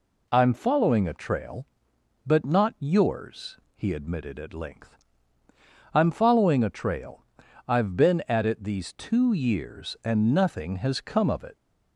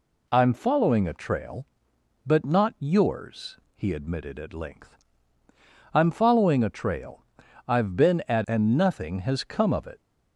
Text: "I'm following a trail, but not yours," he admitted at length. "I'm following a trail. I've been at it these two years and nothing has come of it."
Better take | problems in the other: first | skips "it these two years"; at 8.4 s

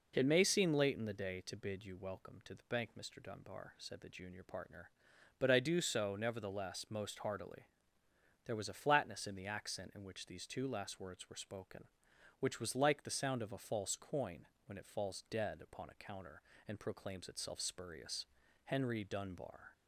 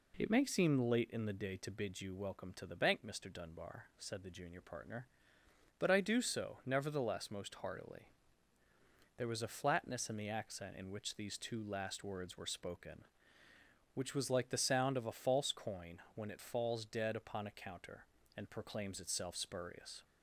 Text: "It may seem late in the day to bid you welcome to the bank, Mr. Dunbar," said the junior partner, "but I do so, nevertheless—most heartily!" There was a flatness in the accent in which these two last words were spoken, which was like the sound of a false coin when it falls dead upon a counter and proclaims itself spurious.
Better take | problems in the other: second | pauses between "coin" and "when"; slight; at 14.4 s; 0.20 s long // goes on to say "Henry Dunbar"; noticeable; from 18.6 s on; 1.0 s long

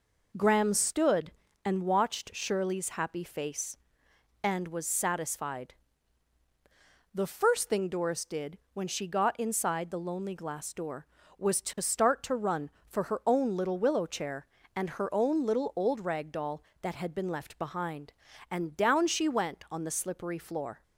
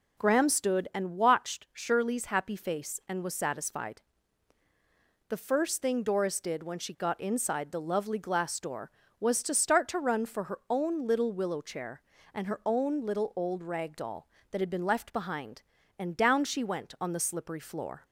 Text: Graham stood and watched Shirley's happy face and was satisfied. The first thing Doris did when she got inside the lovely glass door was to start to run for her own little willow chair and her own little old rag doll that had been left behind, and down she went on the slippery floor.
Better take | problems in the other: second | pauses between "did" and "when"; slight; at 8.5 s; 0.16 s long // says "lonely" for "lovely"; at 9.9 s

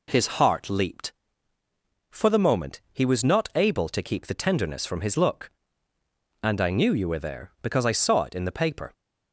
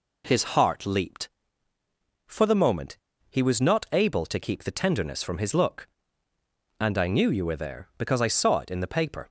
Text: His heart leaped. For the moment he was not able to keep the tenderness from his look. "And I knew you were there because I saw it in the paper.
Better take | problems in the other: first | pauses between "moment" and "he"; slight; at 2.9 s; 0.30 s long

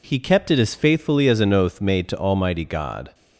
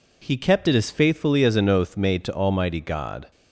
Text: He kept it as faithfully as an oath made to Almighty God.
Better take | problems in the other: neither | none

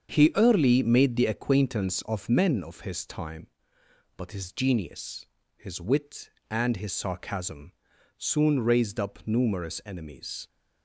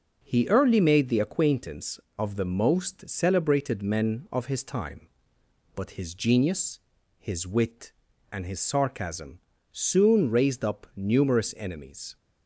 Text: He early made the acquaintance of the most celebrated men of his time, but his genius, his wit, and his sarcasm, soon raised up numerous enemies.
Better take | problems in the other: second | starts louder than the rest; strong; until 1.1 s; 7 dB // skips "the most celebrated"; at 2.2 s

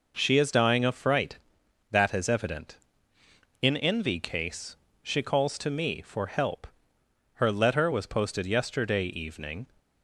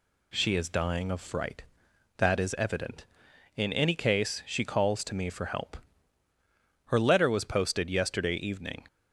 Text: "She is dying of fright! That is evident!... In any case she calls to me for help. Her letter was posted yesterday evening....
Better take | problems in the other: second | says "envy" for "any"; at 3.7 s // pauses between "case" and "she"; slight; at 4.7 s; 0.26 s long

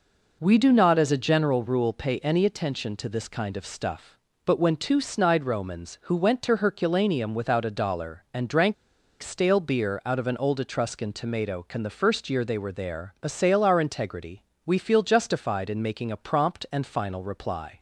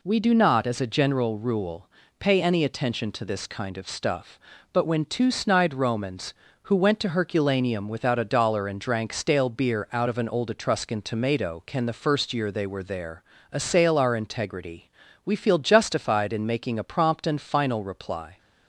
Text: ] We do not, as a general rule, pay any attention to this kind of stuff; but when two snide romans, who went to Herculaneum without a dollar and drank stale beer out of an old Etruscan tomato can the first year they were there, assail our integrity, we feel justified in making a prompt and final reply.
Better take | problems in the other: second | pauses between "drank" and "stale"; noticeable; at 8.7 s; 0.48 s long

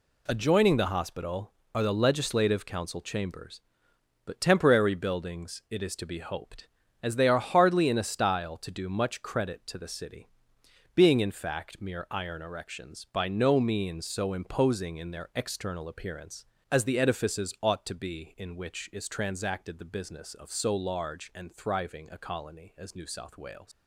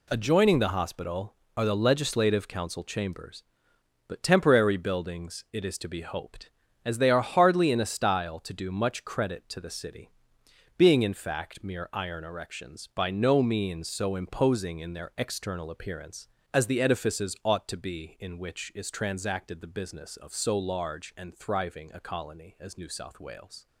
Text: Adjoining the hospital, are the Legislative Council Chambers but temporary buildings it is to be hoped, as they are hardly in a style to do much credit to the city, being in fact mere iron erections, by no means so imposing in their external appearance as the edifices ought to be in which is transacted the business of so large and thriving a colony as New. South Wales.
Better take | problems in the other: second | leaves "Wales" unfinished; at 23.7 s; 130 ms

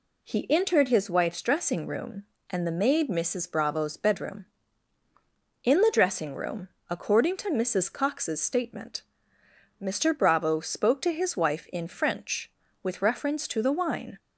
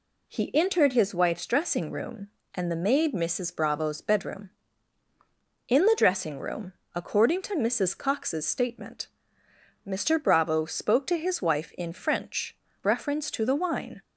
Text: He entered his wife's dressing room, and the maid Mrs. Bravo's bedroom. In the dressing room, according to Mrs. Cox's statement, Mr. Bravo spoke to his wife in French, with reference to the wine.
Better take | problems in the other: first | skips "with"; at 12.6 s

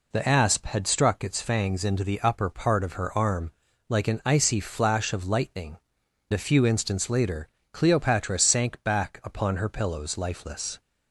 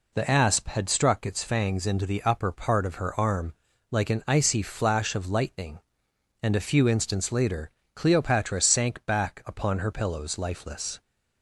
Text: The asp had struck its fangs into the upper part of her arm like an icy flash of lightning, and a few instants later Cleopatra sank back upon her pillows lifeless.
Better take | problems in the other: second | pauses between "arm" and "like"; at 3.5 s; 0.38 s long; also in the second // skips "and"; at 6.0 s // pauses between "later" and "Cleopatra"; slight; at 7.4 s; 0.24 s long; slight in the second

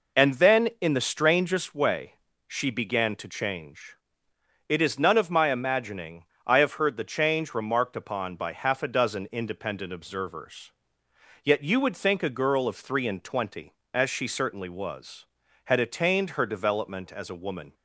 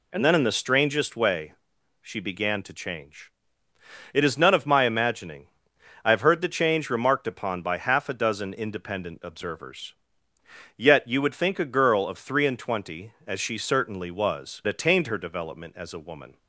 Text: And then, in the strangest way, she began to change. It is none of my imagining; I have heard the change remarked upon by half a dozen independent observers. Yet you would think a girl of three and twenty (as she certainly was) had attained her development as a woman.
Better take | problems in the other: first | skips "had"; at 14.6 s

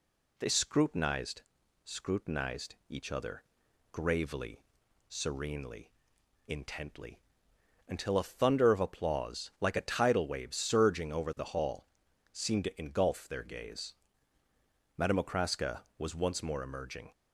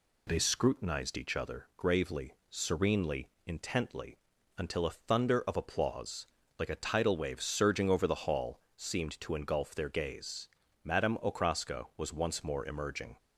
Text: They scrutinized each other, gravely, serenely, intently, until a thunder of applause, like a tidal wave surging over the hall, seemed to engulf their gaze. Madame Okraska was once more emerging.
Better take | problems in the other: second | says "scrutinized" twice; at 1.8 s

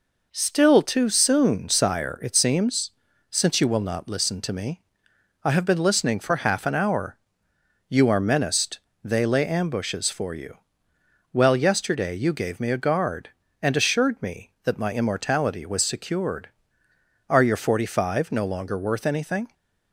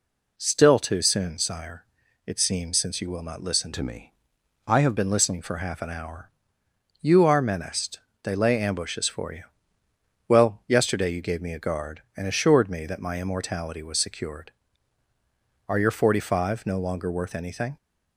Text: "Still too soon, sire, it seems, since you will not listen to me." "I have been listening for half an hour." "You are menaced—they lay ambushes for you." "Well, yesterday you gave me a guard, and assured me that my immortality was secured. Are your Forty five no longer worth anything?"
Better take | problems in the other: first | changes voice from "to" to "have"; from 3.7 to 4.9 s; 1.2 s long

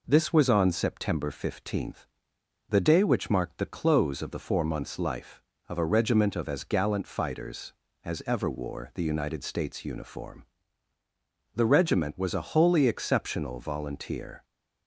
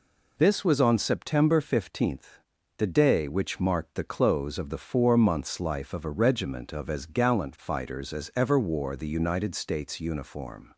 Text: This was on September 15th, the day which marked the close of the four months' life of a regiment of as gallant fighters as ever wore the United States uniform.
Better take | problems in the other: second | goes on to say "The regiment was a wholly exceptional volunteer"; strong; from 11.5 s on; 2.9 s long

